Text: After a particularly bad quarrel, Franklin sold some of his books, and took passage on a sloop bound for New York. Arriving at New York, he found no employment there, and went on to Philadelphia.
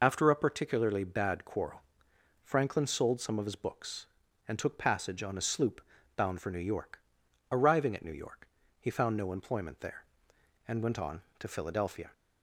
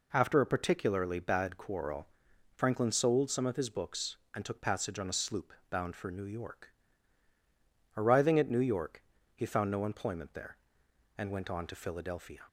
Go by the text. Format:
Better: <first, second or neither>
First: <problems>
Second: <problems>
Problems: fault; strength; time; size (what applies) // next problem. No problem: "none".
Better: second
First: loses the start of "After"; at 0.0 s; 35 ms // pauses between "sloop" and "bound"; slight; at 5.8 s; 0.34 s long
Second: pauses between "sloop" and "bound"; slight; at 5.5 s; 0.16 s long